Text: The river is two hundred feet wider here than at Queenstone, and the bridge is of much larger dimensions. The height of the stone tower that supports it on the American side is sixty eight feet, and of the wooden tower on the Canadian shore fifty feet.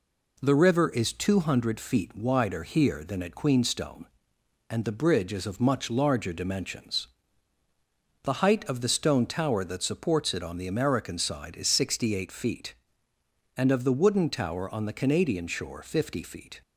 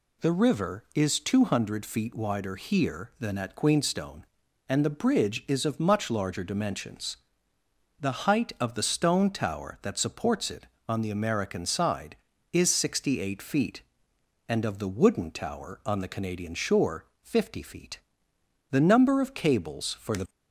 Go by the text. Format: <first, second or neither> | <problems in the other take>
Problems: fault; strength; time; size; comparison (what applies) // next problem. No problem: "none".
first | pauses between "shore" and "fifty"; slight; at 17.0 s; 0.18 s long // goes on to say "The number of cables for the"; from 18.7 s on; 1.5 s long